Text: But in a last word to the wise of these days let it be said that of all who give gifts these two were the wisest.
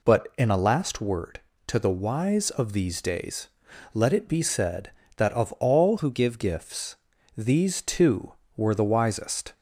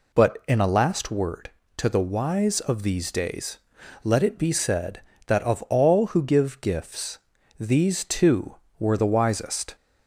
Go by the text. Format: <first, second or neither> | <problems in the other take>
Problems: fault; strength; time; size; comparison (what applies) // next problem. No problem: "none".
second | pauses between "days" and "let"; noticeable; at 3.4 s; 0.46 s long; noticeable in the second // changes voice from "who" to "give"; from 5.9 to 6.3 s; 0.4 s long // pauses between "gifts" and "these"; at 6.9 s; 0.42 s long; also in the second